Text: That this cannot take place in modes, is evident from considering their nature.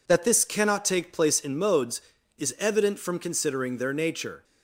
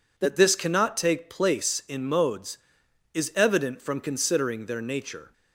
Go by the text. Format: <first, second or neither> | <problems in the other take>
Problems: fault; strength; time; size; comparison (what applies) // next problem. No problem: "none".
neither | none